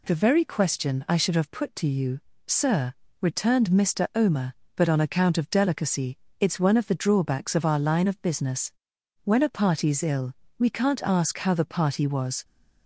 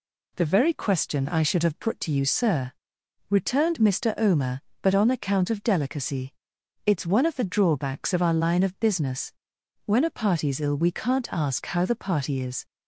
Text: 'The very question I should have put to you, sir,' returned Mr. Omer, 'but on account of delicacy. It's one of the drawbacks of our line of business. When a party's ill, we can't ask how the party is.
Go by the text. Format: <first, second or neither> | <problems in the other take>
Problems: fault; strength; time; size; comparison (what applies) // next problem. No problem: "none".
second | says "was" for "is"; at 12.0 s